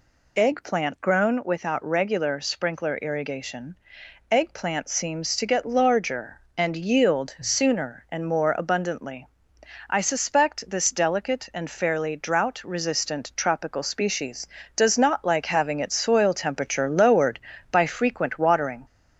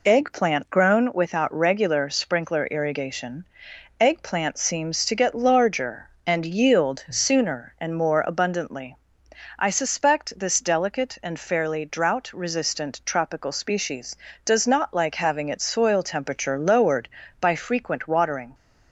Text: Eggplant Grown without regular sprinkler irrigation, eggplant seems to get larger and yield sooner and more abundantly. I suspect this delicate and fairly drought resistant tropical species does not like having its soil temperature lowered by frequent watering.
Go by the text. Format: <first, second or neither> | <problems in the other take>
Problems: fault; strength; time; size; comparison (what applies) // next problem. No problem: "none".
second | gets louder; slight; throughout; 2.5 dB